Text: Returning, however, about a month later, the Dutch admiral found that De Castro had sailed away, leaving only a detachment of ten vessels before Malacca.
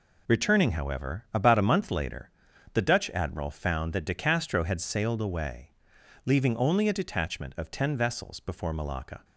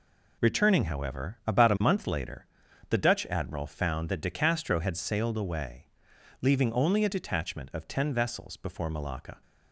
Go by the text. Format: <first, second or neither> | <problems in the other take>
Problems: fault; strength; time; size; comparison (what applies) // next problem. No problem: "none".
neither | none